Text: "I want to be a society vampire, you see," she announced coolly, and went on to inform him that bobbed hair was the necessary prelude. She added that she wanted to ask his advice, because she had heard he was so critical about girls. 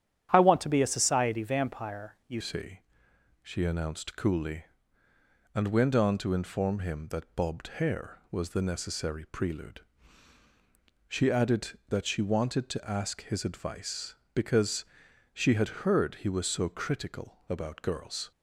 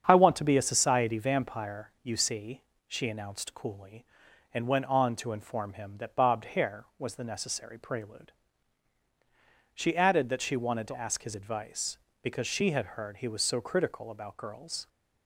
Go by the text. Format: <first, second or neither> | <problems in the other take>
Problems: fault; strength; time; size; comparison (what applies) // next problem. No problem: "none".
second | starts louder than the rest; strong; until 1.3 s; 10 dB; strong in the second // changes voice at "see"; from 2.4 s on; 15.9 s long // pauses between "because" and "she"; noticeable; at 14.8 s; 0.50 s long